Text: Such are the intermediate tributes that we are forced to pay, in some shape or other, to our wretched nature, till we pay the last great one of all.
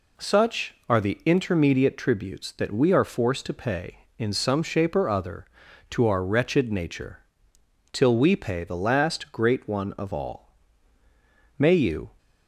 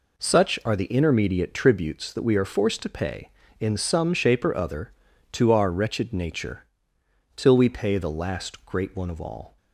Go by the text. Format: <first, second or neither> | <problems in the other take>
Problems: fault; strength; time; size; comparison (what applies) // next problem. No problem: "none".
second | goes on to say "May you"; from 11.5 s on; 0.54 s long